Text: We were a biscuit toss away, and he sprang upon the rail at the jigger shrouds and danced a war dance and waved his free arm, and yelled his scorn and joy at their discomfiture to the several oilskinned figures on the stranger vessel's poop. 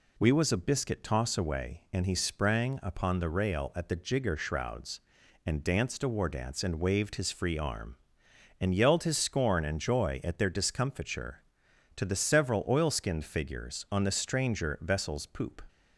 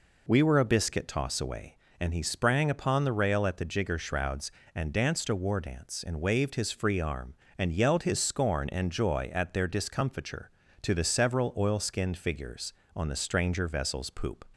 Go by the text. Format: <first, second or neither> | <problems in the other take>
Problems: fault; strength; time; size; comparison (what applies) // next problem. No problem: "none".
second | says "was" for "were"; at 0.3 s